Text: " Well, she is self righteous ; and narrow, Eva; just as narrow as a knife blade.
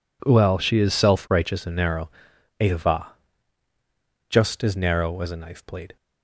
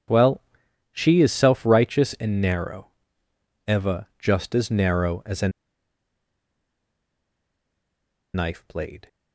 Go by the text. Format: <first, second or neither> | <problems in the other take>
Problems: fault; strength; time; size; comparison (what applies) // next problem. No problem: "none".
first | pauses between "a" and "knife"; strong; at 5.4 s; 2.8 s long